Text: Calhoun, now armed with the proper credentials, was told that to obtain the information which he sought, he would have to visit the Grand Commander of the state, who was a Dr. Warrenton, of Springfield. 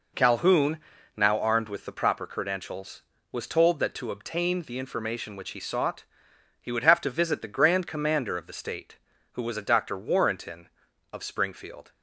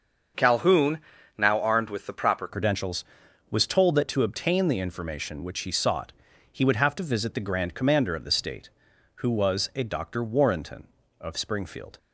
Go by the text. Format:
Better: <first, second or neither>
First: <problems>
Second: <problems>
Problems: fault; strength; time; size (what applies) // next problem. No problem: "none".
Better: first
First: none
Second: starts louder than the rest; until 1.7 s; 6.5 dB // changes voice at "credentials"; from 2.4 s on; 9.5 s long